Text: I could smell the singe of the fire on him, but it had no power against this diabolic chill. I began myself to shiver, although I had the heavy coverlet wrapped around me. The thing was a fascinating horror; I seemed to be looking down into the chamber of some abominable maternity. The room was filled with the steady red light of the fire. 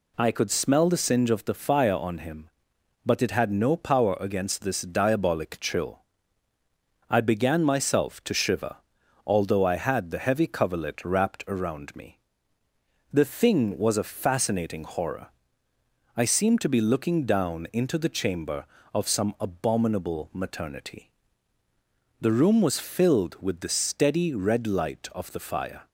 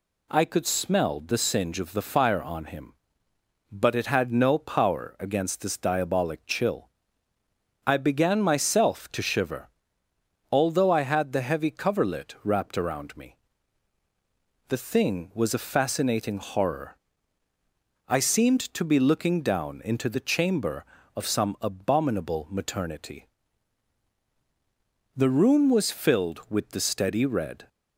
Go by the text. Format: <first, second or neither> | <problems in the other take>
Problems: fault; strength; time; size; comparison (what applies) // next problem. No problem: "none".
first | stops before "light of the fire"; at 27.6 s